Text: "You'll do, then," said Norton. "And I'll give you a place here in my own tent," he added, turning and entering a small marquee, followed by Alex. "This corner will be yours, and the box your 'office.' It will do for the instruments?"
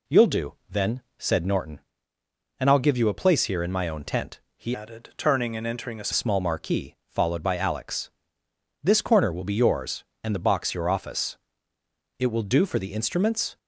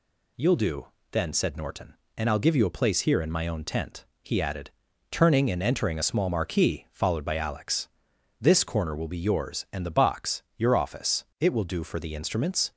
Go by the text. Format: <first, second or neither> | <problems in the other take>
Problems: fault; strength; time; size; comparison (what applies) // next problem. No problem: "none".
second | changes voice from "added" to "a"; from 4.7 to 6.0 s; 1.3 s long